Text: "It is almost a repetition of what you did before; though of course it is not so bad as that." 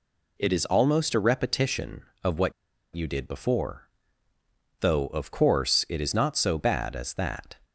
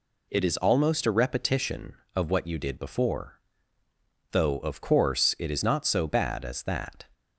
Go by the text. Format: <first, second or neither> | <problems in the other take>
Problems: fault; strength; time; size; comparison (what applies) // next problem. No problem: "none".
second | pauses between "what" and "you"; at 2.5 s; 0.42 s long